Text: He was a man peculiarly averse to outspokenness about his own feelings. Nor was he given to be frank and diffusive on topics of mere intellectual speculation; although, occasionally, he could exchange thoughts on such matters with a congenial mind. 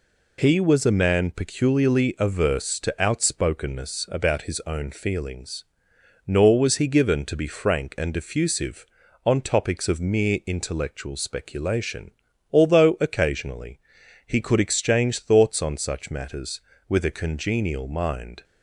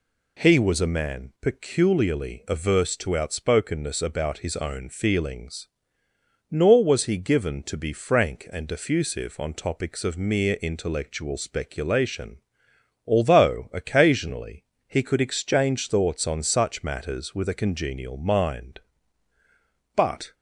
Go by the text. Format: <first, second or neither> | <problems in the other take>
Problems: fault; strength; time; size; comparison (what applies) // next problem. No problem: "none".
first | goes on to say "But"; slight; from 19.9 s on; 0.38 s long